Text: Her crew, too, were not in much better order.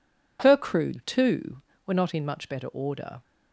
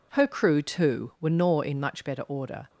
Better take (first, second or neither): first